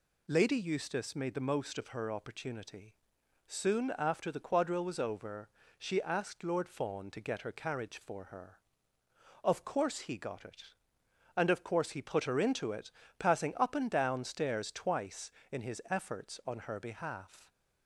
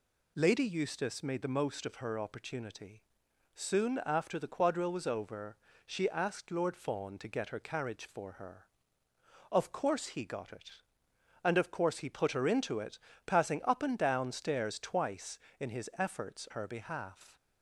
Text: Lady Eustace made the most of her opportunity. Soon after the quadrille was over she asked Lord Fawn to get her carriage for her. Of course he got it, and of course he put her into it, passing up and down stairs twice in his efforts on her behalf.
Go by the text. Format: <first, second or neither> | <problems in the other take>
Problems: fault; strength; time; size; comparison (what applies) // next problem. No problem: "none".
first | pauses between "over" and "she"; slight; at 5.5 s; 0.30 s long; slight in the first // skips "on"; at 16.4 s